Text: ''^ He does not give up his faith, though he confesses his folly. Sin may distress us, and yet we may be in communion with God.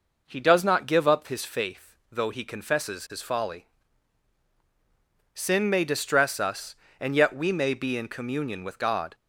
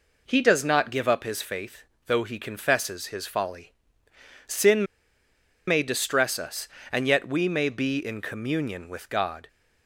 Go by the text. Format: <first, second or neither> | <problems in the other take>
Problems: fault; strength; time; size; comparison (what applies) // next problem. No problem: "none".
first | pauses between "Sin" and "may"; noticeable; at 4.8 s; 0.83 s long